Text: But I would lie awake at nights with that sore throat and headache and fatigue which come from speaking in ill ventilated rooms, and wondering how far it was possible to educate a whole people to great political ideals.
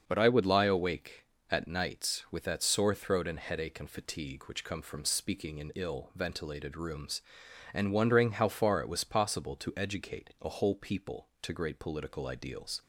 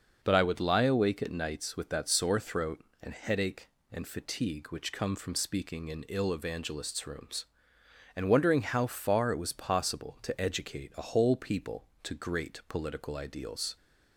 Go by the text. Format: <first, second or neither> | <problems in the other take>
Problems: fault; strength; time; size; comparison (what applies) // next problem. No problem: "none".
first | starts louder than the rest; noticeable; until 1.2 s; 6 dB; also in the first // says "evangelists" for "ventilated"; at 6.3 s